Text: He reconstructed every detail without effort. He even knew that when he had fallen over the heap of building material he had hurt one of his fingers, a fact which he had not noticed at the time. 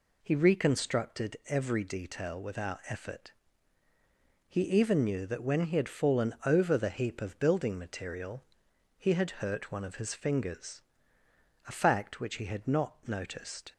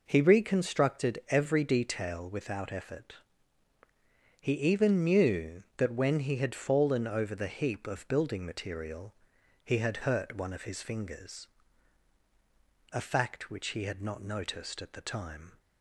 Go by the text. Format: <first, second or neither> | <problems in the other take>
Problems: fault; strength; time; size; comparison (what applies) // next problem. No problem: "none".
second | pauses between "material" and "he"; noticeable; at 8.4 s; 0.54 s long; noticeable in the second // stops before "at the time"; at 13.7 s